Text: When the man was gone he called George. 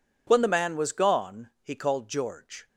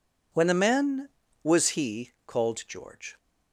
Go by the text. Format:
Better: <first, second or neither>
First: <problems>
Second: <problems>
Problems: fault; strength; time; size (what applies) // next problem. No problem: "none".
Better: first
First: none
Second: skips "gone"; at 1.6 s